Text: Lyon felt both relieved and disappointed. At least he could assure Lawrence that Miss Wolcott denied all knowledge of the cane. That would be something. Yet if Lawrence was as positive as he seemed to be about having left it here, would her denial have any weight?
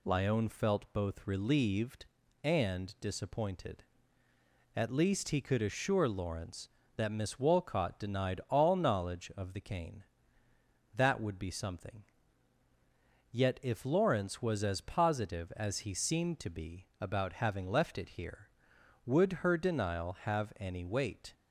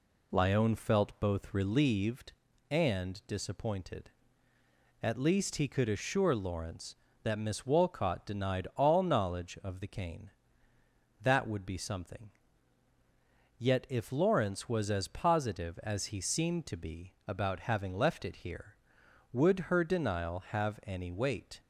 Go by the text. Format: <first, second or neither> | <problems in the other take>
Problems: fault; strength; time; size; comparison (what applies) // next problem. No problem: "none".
first | starts louder than the rest; slight; until 1.9 s; 2 dB